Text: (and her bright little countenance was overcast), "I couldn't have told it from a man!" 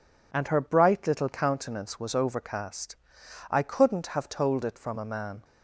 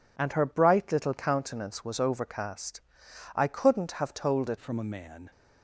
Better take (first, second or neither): first